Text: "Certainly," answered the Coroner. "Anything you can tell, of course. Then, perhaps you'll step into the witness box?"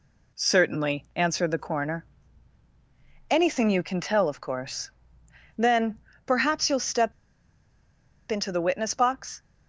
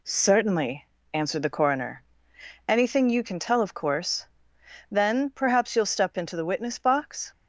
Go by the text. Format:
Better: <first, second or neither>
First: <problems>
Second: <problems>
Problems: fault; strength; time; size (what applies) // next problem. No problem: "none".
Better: second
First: pauses between "step" and "into"; at 7.1 s; 1.1 s long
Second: none